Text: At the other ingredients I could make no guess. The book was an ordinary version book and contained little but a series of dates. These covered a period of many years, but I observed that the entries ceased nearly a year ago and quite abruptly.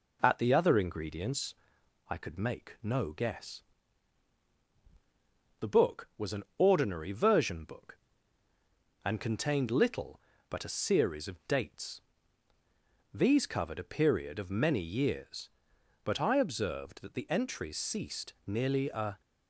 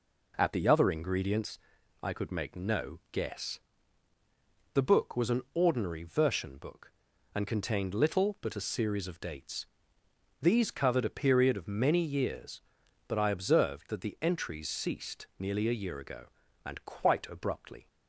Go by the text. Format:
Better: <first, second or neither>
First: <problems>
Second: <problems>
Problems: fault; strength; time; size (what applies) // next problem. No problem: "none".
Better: second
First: pauses between "ingredients" and "I"; noticeable; at 1.5 s; 0.54 s long // pauses between "an" and "ordinary"; slight; at 6.4 s; 0.16 s long // stops before "year ago and quite abruptly"; at 19.2 s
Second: pauses between "ingredients" and "I"; at 1.5 s; 0.44 s long